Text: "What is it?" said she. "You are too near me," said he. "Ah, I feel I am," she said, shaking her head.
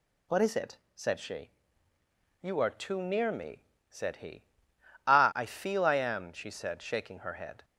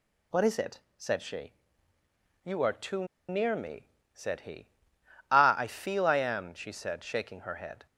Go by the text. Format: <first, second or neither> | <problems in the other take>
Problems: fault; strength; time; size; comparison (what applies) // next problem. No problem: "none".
first | pauses between "too" and "near"; slight; at 3.0 s; 0.24 s long